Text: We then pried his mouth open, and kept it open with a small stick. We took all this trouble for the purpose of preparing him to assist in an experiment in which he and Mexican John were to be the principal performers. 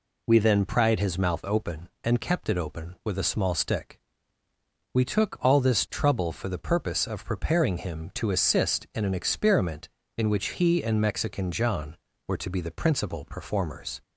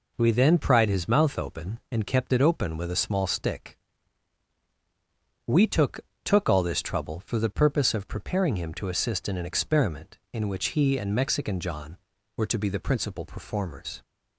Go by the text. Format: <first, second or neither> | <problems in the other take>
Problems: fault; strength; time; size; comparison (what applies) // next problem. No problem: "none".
first | says "took" twice; at 6.2 s